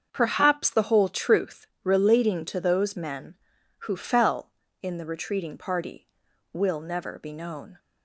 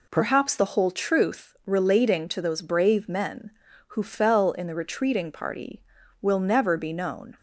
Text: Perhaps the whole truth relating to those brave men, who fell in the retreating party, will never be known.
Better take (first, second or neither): second